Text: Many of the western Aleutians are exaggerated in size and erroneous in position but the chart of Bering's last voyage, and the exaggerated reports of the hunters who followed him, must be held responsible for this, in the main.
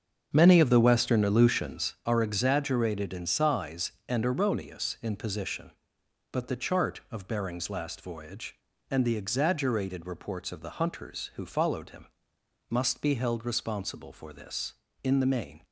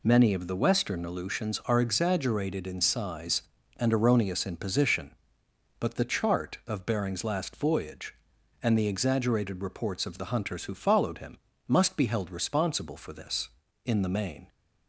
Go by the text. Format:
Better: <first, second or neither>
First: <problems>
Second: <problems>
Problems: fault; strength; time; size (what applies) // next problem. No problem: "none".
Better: second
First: starts louder than the rest; until 2.0 s; 7 dB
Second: none